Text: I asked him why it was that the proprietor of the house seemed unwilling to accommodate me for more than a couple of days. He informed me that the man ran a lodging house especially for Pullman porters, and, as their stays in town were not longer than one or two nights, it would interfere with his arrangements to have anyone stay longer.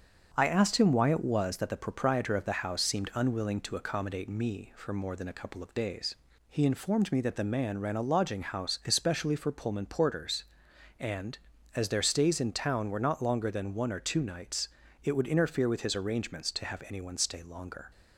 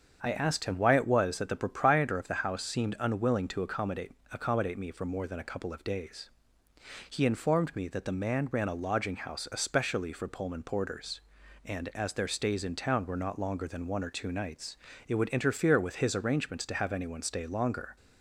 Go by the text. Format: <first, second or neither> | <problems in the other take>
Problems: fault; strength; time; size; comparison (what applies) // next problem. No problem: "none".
first | starts louder than the rest; strong; until 1.2 s; 7 dB; strong in the first // says "accommodate" twice; at 4.3 s